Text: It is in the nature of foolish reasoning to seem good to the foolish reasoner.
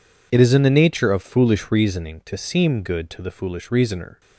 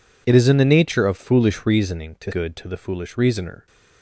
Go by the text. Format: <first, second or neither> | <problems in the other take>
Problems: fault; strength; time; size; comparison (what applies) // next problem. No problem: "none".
first | skips "seem"; at 2.3 s